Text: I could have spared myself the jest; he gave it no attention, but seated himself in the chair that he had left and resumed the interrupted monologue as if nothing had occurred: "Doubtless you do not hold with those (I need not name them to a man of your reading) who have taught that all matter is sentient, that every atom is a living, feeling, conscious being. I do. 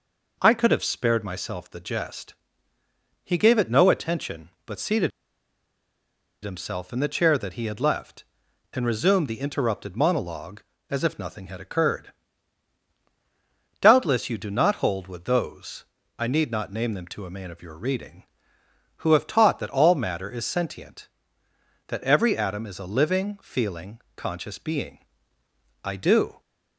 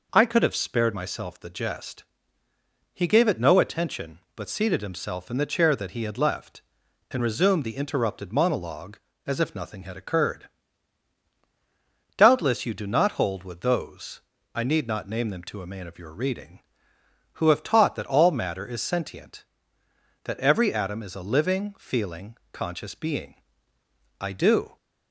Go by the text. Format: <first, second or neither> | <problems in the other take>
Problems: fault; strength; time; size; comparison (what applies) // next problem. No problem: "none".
second | pauses between "seated" and "himself"; strong; at 5.0 s; 1.3 s long